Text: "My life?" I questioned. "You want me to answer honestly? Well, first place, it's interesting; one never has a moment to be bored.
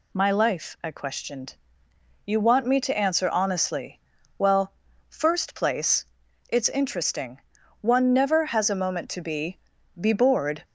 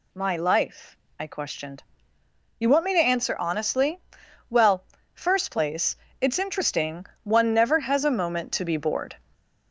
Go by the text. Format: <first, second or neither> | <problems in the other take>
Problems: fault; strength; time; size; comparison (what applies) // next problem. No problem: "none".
second | says "be" twice; at 10.0 s